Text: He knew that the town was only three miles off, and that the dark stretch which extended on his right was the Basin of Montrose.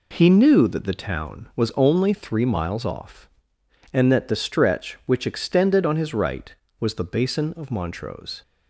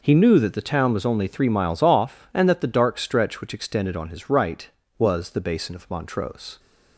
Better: second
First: skips "dark"; at 4.3 s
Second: none

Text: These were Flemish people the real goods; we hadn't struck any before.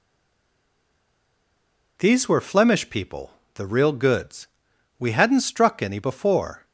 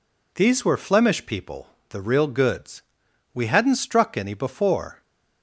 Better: second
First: stays silent before the first word; noticeable; until 1.9 s; 1.9 s long // pauses between "people" and "the"; slight; at 3.3 s; 0.24 s long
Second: pauses between "people" and "the"; slight; at 1.6 s; 0.23 s long

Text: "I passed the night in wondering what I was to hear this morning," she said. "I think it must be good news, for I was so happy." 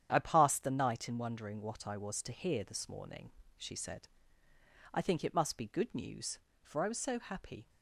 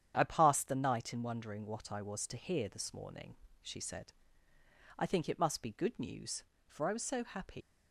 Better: first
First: starts louder than the rest; strong; until 1.1 s; 9 dB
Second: starts louder than the rest; strong; until 1.1 s; 9 dB // leaves "happy" unfinished; at 7.6 s; 125 ms

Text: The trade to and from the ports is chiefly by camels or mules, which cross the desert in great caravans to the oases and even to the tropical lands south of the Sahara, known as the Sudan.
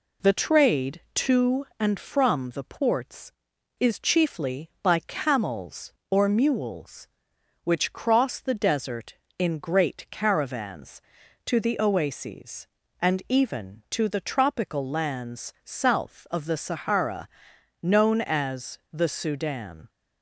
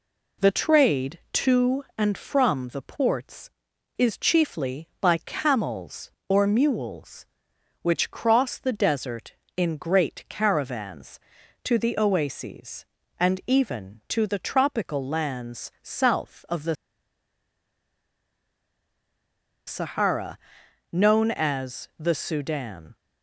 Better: first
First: none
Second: pauses between "the" and "Sahara"; strong; at 16.7 s; 2.9 s long

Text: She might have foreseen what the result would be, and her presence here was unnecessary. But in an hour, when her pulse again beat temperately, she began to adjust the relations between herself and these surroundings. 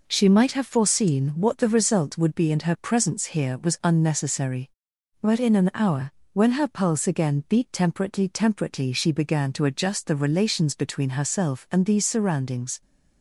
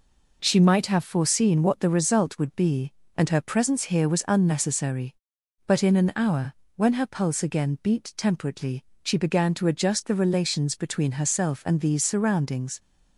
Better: second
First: says "temperately" twice; at 8.2 s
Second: none

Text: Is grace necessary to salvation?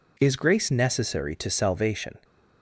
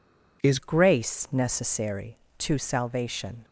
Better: first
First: none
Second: changes voice at "grace"; from 0.5 s on; 2.9 s long

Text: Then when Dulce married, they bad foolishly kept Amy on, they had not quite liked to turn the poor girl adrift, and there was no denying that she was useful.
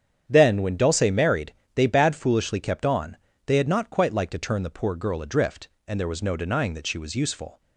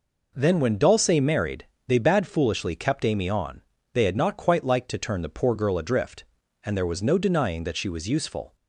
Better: second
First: starts louder than the rest; strong; until 1.2 s; 8.5 dB // skips "Amy"; at 2.8 s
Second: none

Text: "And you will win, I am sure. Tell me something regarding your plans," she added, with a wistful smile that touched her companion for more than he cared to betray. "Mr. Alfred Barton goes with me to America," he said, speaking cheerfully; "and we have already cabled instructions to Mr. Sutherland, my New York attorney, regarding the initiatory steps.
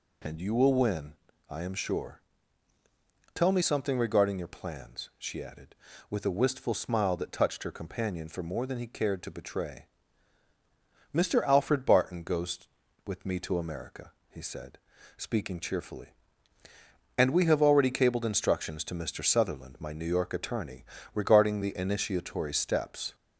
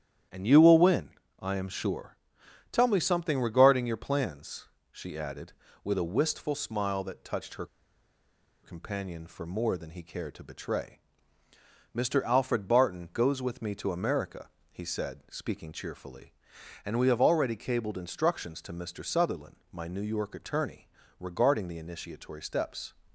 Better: first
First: none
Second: starts louder than the rest; strong; until 1.6 s; 10.5 dB // pauses between "her" and "companion"; at 7.6 s; 0.98 s long

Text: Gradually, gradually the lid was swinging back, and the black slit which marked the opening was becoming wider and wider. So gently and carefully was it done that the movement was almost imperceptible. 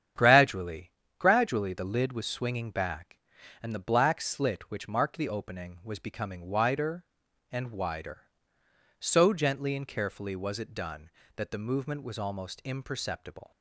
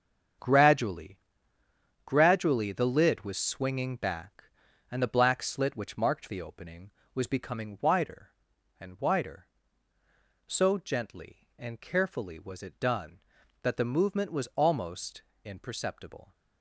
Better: first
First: starts louder than the rest; strong; until 1.4 s; 9 dB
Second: gets quieter; strong; throughout; 9.5 dB // starts louder than the rest; strong; until 2.2 s; 7.5 dB // pauses between "almost" and "imperceptible"; slight; at 15.2 s; 0.22 s long

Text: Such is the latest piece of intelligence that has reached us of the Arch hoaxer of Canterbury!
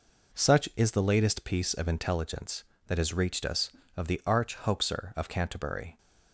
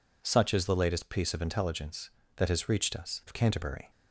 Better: first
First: none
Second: skips "of the Arch hoaxer"; at 3.2 s

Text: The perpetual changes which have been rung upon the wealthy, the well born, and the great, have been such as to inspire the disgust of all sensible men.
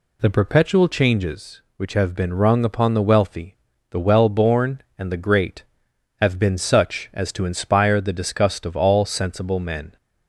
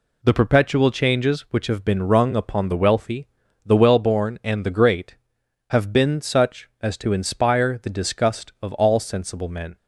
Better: first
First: none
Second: gets quieter; noticeable; throughout; 6 dB

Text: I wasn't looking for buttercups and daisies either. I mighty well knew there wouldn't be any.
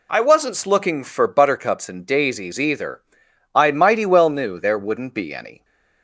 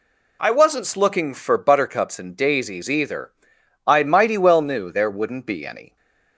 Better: neither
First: none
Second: none

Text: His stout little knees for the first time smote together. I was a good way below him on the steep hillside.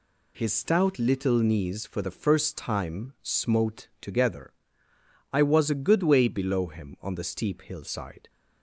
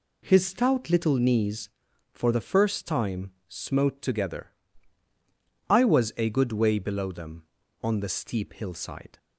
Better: first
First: none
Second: pauses between "time" and "smote"; slight; at 3.3 s; 0.18 s long // says "them" for "him"; at 7.0 s

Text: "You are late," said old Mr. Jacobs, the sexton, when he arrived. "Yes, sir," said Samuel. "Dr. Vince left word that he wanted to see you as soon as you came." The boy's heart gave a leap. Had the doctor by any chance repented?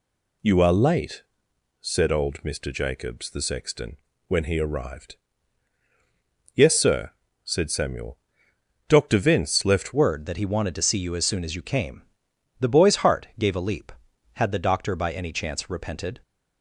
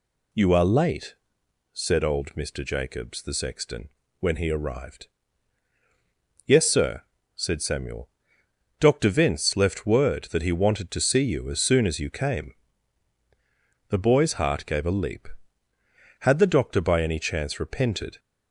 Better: second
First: changes voice at "word"; from 9.9 s on; 6.3 s long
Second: none

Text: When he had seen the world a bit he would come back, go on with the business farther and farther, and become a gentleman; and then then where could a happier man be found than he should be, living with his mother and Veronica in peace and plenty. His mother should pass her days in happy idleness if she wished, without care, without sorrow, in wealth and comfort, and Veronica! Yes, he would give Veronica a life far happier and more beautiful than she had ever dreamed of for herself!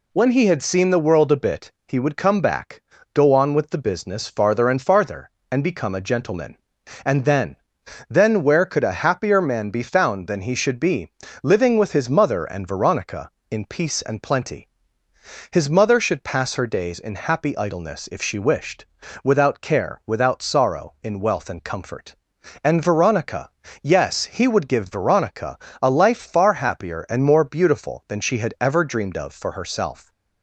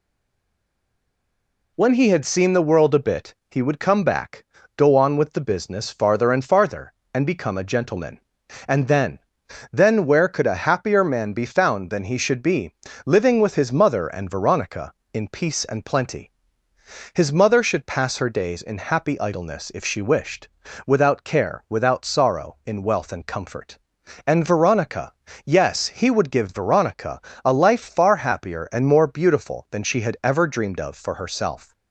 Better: first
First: pauses between "bit" and "he"; slight; at 1.7 s; 0.16 s long // pauses between "then" and "then"; noticeable; at 7.5 s; 0.54 s long // pauses between "Veronica" and "a"; slight; at 25.5 s; 0.24 s long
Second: stays silent before the first word; noticeable; until 1.7 s; 1.7 s long // pauses between "bit" and "he"; slight; at 3.3 s; 0.16 s long // pauses between "then" and "then"; noticeable; at 9.1 s; 0.54 s long // pauses between "Veronica" and "a"; slight; at 27.2 s; 0.24 s long

